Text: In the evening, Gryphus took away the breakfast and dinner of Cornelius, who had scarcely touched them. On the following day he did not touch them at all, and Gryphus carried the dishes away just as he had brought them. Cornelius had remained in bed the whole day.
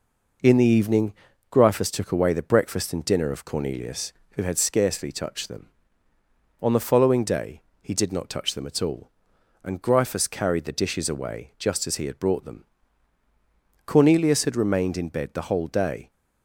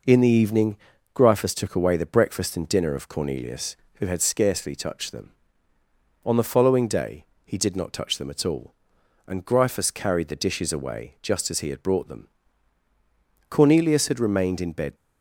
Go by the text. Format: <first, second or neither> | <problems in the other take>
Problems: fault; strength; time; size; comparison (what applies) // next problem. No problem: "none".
first | pauses between "day" and "he"; slight; at 7.2 s; 0.20 s long; slight in the first // stops before "the whole day"; at 14.9 s